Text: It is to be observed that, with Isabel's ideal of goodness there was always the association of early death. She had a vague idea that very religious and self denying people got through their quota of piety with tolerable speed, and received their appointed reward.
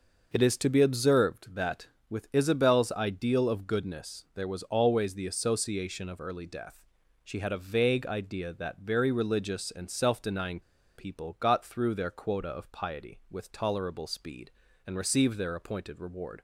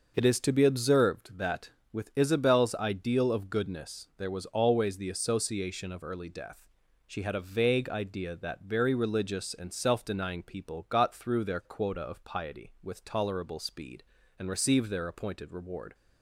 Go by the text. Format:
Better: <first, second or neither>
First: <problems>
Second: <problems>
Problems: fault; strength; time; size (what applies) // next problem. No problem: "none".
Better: second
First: starts louder than the rest; noticeable; until 1.3 s; 6 dB // pauses between "denying" and "people"; at 10.6 s; 0.36 s long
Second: starts louder than the rest; noticeable; until 1.1 s; 6 dB